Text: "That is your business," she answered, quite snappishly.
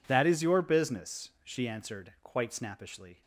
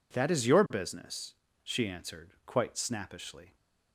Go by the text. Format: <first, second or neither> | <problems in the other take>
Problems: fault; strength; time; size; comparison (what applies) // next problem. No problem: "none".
neither | none